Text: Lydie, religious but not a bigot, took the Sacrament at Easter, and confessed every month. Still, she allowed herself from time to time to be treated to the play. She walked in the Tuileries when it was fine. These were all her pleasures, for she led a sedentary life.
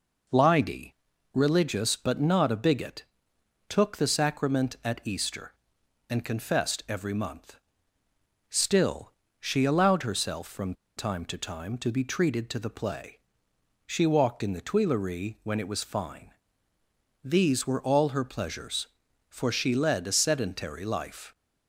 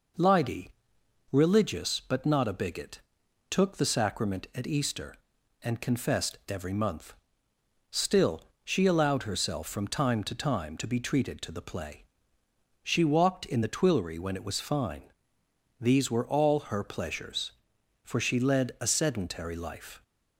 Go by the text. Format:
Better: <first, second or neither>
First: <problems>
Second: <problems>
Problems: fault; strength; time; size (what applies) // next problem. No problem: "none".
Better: second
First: pauses between "from" and "time"; slight; at 10.7 s; 0.23 s long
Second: none